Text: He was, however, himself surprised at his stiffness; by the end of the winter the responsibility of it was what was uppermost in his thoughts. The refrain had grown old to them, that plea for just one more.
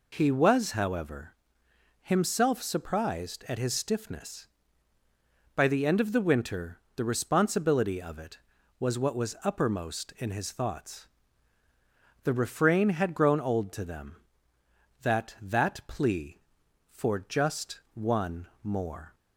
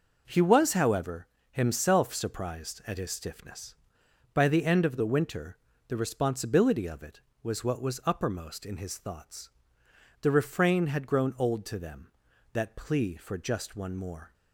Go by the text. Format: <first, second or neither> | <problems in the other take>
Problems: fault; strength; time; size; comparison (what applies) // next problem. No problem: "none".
second | pauses between "winter" and "the"; slight; at 6.7 s; 0.20 s long; slight in the second // says "that" twice; at 15.4 s